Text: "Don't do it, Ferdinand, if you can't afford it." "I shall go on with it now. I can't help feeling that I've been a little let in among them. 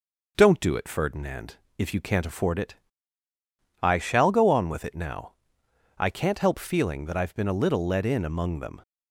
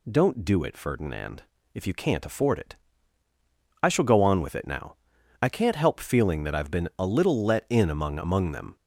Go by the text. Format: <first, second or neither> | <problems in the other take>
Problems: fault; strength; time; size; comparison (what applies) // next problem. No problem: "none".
first | says "among" twice; at 8.1 s